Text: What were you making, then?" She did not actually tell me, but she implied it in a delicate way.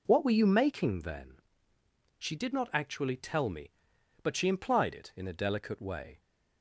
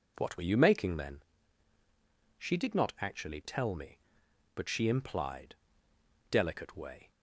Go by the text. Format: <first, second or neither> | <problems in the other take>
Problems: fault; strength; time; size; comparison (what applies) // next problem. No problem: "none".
first | skips "it in a"; at 5.9 s